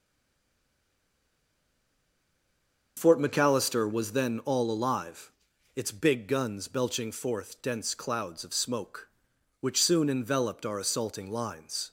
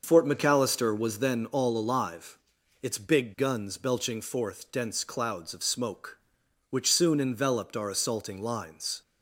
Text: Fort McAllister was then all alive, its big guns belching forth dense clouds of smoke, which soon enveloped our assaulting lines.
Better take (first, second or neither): second